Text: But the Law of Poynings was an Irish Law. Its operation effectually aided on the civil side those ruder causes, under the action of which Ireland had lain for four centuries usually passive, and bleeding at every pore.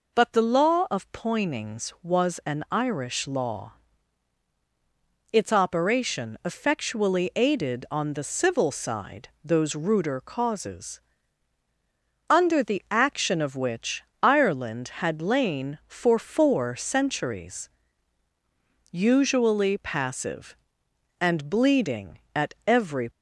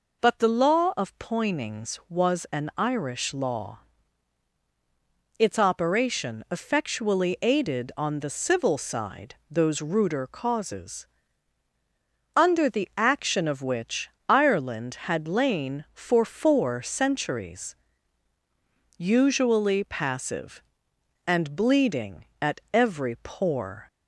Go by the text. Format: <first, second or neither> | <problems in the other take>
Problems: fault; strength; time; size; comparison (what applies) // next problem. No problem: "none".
second | pauses between "which" and "Ireland"; slight; at 14.0 s; 0.20 s long; slight in the second // pauses between "centuries" and "usually"; strong; at 17.6 s; 1.2 s long; strong in the second // stops before "pore"; at 23.0 s